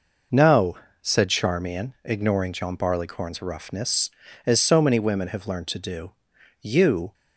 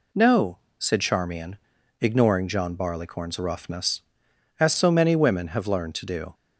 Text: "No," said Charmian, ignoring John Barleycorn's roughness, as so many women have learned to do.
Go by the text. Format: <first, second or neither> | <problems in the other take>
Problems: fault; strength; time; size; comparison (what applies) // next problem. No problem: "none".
second | goes on to say "You"; from 6.5 s on; 0.54 s long